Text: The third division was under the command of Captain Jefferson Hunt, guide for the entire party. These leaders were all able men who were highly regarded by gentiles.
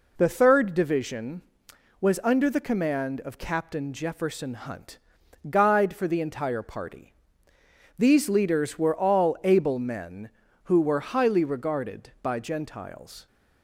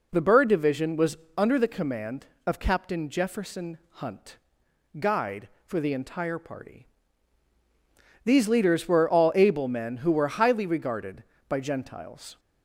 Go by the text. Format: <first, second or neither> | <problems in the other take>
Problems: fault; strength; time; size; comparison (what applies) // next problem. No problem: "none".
first | says "bird" for "third"; at 0.2 s // pauses between "was" and "under"; slight; at 1.1 s; 0.20 s long // pauses between "Jefferson" and "Hunt"; slight; at 3.7 s; 0.16 s long